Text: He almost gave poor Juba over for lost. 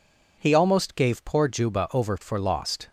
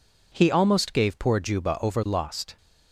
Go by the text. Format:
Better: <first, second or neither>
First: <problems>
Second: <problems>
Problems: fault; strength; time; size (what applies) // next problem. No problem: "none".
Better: first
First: none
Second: skips "for"; at 2.0 s